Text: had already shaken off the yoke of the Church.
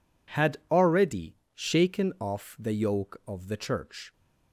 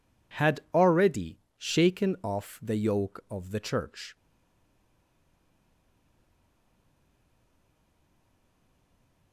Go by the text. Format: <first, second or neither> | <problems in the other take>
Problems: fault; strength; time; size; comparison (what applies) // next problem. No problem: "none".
first | pauses between "already" and "shaken"; slight; at 1.3 s; 0.20 s long; slight in the first // stays silent after the last word; strong; from 4.1 s on; 5.2 s long